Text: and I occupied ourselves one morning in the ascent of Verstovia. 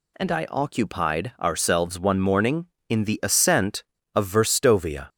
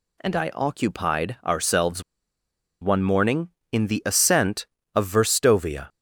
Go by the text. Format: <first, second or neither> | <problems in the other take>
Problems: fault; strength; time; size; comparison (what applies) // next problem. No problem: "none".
first | pauses between "ourselves" and "one"; noticeable; at 2.0 s; 0.79 s long